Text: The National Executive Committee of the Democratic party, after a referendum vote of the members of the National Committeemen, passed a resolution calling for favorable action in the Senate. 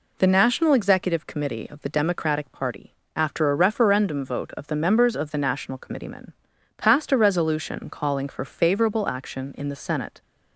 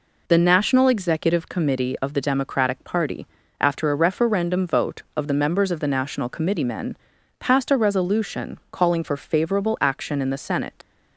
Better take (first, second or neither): first